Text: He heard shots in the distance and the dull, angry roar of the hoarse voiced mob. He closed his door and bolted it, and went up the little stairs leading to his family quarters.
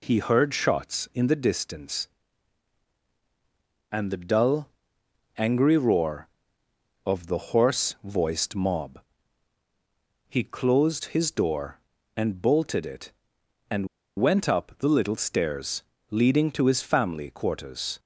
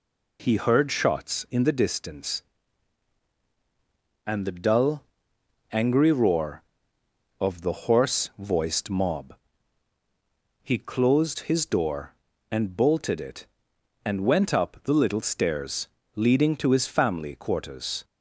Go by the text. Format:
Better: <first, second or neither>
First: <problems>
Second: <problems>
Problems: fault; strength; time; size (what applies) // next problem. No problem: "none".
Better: second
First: pauses between "and" and "went"; slight; at 13.8 s; 0.31 s long // pauses between "stairs" and "leading"; slight; at 15.8 s; 0.26 s long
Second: pauses between "stairs" and "leading"; slight; at 15.8 s; 0.26 s long